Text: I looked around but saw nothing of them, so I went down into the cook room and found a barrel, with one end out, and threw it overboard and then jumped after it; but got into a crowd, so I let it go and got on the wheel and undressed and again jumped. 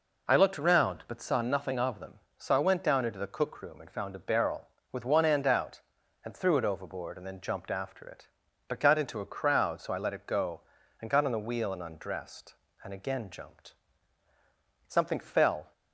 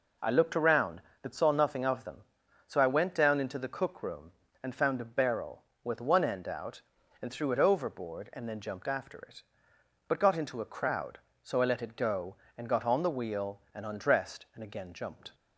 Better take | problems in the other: second | goes on to say "Something fell"; noticeable; from 14.8 s on; 0.86 s long

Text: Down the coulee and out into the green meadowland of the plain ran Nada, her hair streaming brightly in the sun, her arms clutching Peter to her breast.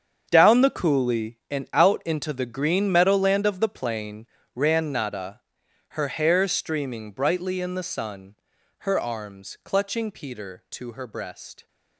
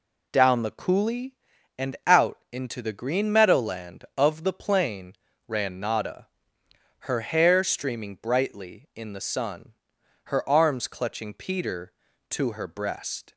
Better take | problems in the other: second | gets quieter; strong; throughout; 13.5 dB // pauses between "plain" and "ran"; slight; at 4.2 s; 0.28 s long; slight in the second

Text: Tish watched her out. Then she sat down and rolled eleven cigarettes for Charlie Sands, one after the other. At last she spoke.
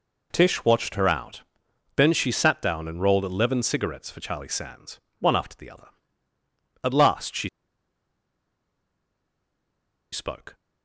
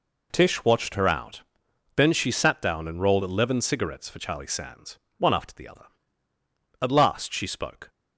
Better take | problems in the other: second | pauses between "she" and "spoke"; strong; at 7.4 s; 2.6 s long

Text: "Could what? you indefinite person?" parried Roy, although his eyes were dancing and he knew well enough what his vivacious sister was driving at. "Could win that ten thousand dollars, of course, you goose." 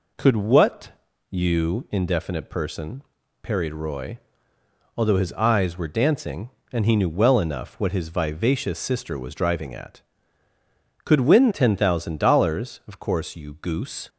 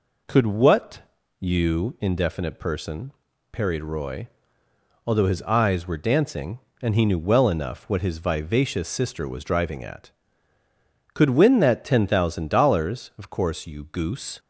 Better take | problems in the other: second | skips "that"; at 11.5 s

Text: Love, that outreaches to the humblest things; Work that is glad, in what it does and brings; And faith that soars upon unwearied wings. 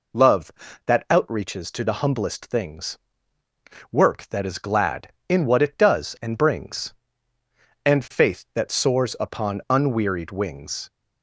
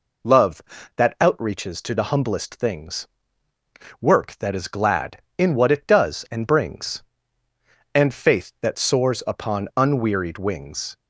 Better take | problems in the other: neither | none

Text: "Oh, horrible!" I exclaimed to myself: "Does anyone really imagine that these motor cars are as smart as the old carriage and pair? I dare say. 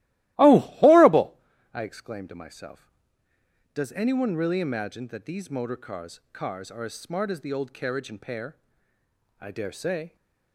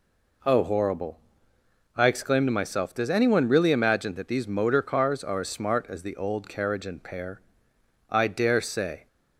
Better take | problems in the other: second | starts louder than the rest; strong; until 1.3 s; 17 dB // says "cars" twice; at 6.3 s

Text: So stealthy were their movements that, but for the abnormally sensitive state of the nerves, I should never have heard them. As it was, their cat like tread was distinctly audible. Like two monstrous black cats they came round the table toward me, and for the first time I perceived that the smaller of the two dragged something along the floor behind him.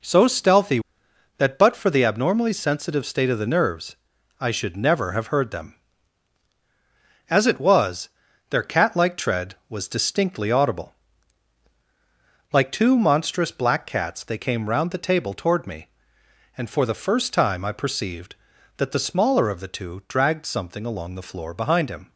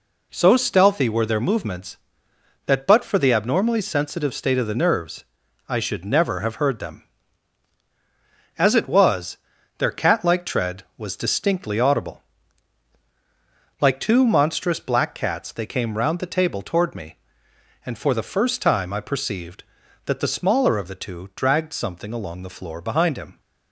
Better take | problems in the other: second | skips "were their movements"; at 1.0 s

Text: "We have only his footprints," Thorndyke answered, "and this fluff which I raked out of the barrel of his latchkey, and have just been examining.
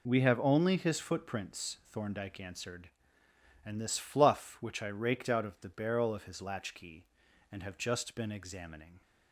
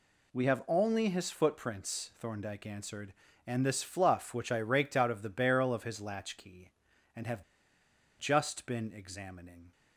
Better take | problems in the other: first | pauses between "have" and "just"; noticeable; at 7.4 s; 0.77 s long

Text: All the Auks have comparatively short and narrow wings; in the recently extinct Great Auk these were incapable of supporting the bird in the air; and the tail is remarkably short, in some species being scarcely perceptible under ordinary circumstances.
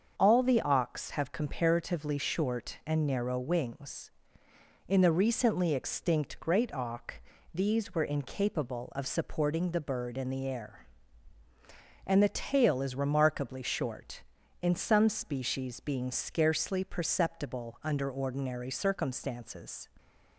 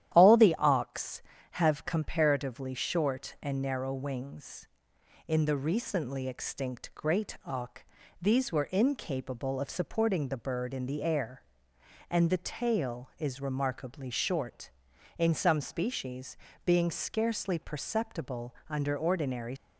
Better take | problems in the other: first | starts louder than the rest; strong; until 1.1 s; 11.5 dB; also in the first // pauses between "Auk" and "these"; at 7.8 s; 0.38 s long; slight in the first // pauses between "species" and "being"; slight; at 16.3 s; 0.30 s long // stops before "circumstances"; at 19.5 s

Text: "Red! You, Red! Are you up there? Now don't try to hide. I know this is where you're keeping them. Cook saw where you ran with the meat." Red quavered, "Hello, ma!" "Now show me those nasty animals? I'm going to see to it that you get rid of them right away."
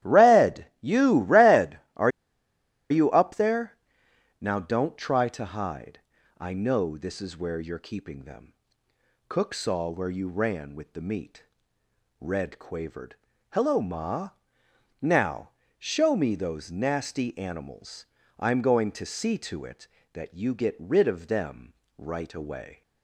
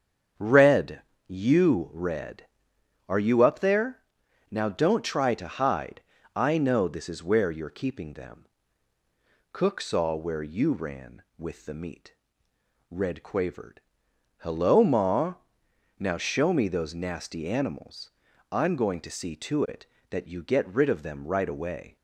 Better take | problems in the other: second | starts louder than the rest; strong; until 1.1 s; 13 dB; strong in the second // pauses between "Are" and "you"; noticeable; at 2.1 s; 0.80 s long // pauses between "Now" and "show"; slight; at 15.5 s; 0.26 s long // pauses between "them" and "right"; slight; at 21.7 s; 0.22 s long

